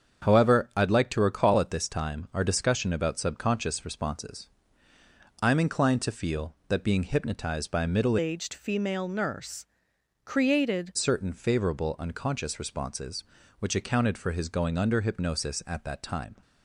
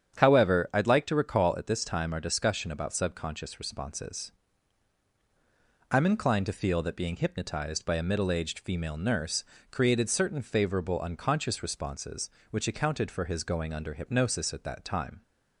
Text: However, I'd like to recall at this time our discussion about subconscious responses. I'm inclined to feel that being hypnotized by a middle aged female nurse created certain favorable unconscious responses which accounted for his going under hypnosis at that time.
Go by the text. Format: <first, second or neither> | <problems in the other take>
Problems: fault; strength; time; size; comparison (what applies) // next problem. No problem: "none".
second | starts louder than the rest; strong; until 1.3 s; 7.5 dB; strong in the second // changes voice from "aged" to "created"; from 8.1 to 10.9 s; 2.8 s long // pauses between "nurse" and "created"; noticeable; at 9.6 s; 0.58 s long; slight in the second